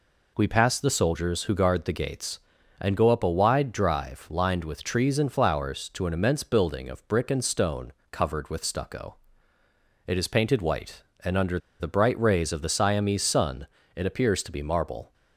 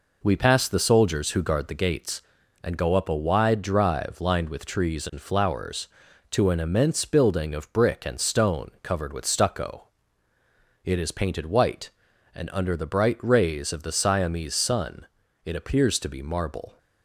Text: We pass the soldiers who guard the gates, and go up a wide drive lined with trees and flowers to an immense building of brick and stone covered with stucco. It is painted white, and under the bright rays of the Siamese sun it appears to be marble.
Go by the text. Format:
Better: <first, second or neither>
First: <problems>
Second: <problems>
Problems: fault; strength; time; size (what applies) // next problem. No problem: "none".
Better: second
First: pauses between "stone" and "covered"; slight; at 7.9 s; 0.18 s long // pauses between "under" and "the"; slight; at 11.5 s; 0.20 s long // pauses between "sun" and "it"; slight; at 13.6 s; 0.30 s long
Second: pauses between "sun" and "it"; at 15.0 s; 0.38 s long